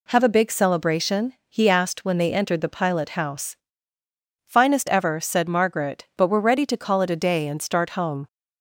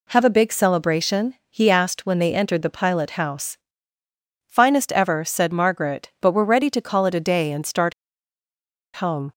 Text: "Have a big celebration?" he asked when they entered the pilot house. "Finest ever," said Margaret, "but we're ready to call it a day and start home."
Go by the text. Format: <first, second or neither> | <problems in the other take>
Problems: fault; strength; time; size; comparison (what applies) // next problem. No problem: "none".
first | pauses between "start" and "home"; at 7.9 s; 1.0 s long